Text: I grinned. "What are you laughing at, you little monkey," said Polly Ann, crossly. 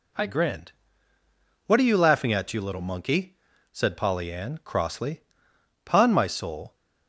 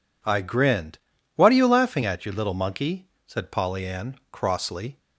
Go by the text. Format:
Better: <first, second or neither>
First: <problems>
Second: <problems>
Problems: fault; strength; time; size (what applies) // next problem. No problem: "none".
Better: second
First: goes on to say "Pon my soul"; noticeable; from 5.8 s on; 0.90 s long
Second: none